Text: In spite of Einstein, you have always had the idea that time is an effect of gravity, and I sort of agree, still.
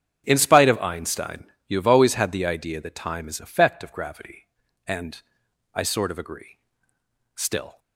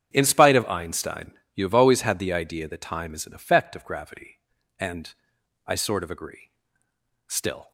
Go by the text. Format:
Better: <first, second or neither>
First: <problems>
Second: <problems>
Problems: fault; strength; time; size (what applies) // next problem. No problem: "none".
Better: second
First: starts louder than the rest; strong; until 1.2 s; 8 dB // skips "an"; at 3.3 s // pauses between "and" and "I"; noticeable; at 5.2 s; 0.52 s long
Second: starts louder than the rest; strong; until 1.1 s; 8.5 dB // pauses between "and" and "I"; noticeable; at 5.1 s; 0.52 s long